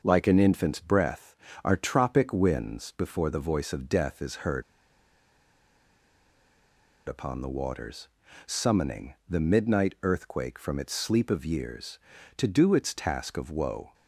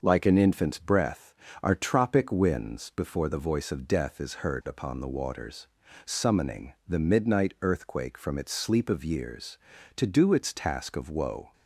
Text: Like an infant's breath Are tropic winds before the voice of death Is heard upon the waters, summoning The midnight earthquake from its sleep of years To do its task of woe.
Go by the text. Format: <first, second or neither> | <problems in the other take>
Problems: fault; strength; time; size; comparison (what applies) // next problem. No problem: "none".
second | pauses between "heard" and "upon"; strong; at 4.6 s; 2.4 s long